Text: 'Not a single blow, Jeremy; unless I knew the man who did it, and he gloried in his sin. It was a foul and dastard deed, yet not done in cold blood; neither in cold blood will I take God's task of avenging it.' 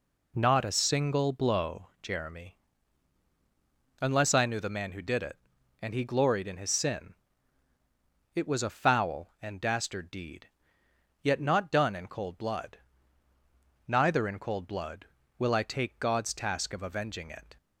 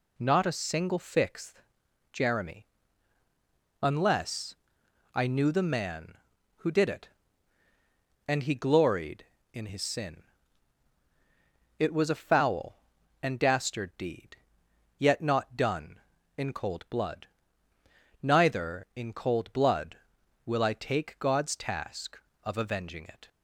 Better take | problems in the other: first | says "fixth" for "blow"; at 0.9 s // pauses between "unless" and "I"; noticeable; at 4.5 s; 0.60 s long

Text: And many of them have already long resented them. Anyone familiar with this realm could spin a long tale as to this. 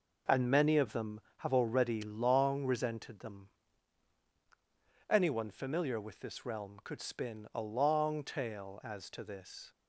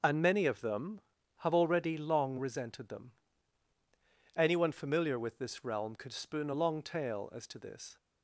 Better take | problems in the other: first | starts louder than the rest; until 1.4 s; 6 dB // says "spoon" for "spin"; at 6.1 s

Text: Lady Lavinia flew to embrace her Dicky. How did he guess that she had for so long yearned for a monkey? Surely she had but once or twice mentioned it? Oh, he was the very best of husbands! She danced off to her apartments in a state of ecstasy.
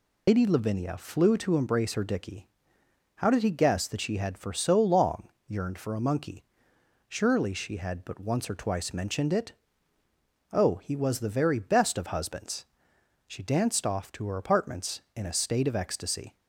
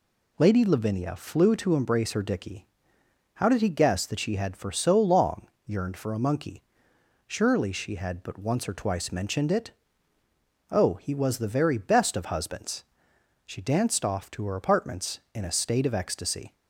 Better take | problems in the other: second | loses the start of "Lady"; at 0.2 s; 95 ms // pauses between "long" and "yearned"; slight; at 5.2 s; 0.18 s long; slight in the second

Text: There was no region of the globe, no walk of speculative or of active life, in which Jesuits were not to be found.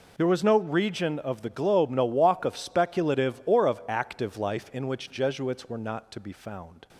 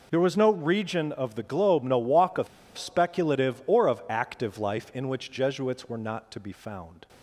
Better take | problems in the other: first | pauses between "of" and "speculative"; slight; at 2.4 s; 0.30 s long

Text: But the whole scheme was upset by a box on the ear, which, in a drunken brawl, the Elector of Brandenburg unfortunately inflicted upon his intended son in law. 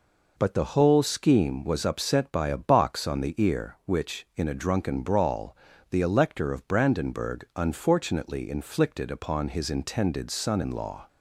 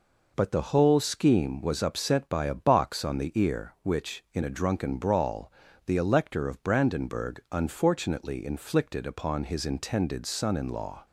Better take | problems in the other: neither | none

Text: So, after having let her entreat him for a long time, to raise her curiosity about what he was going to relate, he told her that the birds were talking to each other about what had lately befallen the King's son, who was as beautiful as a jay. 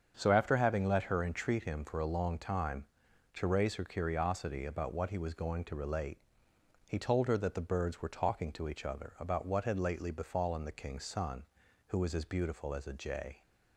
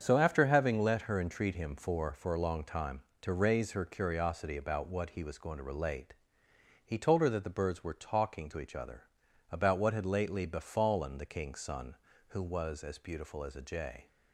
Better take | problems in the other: first | starts louder than the rest; strong; until 1.0 s; 7.5 dB; strong in the first // says "for" twice; at 2.1 s // pauses between "other" and "about"; noticeable; at 9.0 s; 0.48 s long

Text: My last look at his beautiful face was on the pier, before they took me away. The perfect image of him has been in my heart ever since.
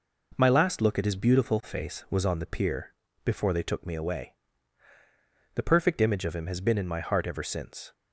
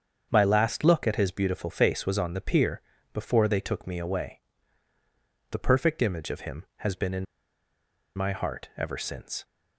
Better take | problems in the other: first | starts louder than the rest; strong; until 1.3 s; 7 dB // pauses between "in" and "my"; noticeable; at 7.2 s; 0.91 s long

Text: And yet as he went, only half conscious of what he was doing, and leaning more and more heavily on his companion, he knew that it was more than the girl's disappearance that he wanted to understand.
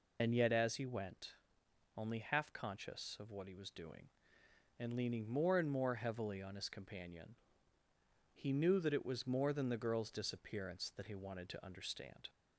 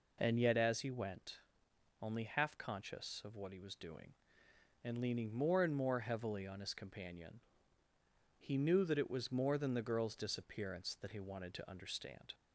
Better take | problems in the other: second | loses the start of "And"; at 0.1 s; 70 ms

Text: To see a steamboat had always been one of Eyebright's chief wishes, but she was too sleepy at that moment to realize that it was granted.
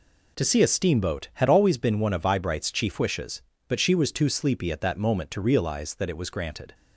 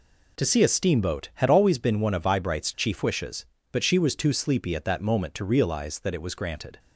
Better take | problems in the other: neither | none

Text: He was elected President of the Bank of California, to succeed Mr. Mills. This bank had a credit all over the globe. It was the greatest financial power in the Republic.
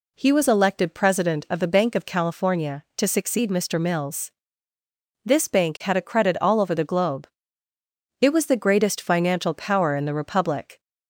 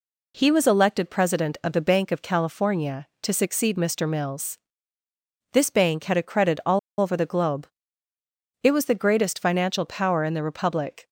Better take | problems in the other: first | pauses between "all" and "over"; slight; at 6.7 s; 0.20 s long

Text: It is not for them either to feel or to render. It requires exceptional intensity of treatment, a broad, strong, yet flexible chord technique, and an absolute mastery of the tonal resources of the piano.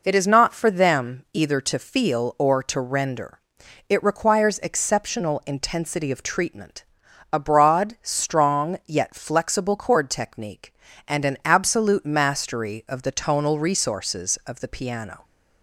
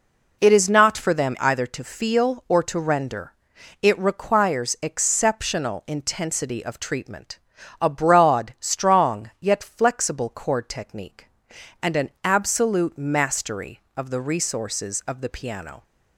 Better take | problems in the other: first | skips "tonal"; at 14.2 s

